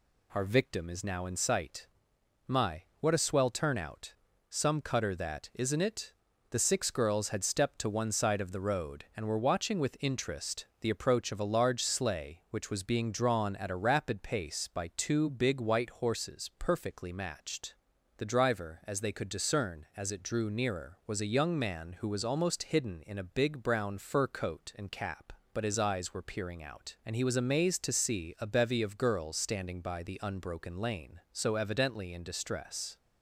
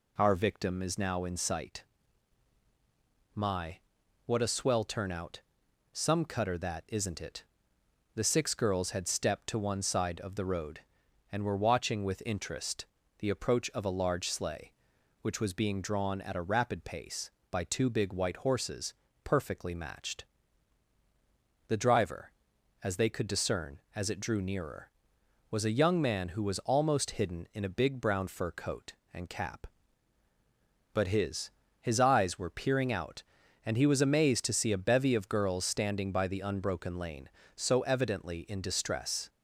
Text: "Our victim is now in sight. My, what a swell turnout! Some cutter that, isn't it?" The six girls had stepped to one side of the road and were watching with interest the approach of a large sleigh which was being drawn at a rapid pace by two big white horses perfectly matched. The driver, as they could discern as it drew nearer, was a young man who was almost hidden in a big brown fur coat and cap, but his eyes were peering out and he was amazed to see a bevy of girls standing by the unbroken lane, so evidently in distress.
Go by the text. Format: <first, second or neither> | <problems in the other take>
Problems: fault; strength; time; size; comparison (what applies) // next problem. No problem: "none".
first | pauses between "interest" and "the"; slight; at 12.8 s; 0.32 s long // pauses between "horses" and "perfectly"; slight; at 18.9 s; 0.32 s long // says "his" twice; at 31.8 s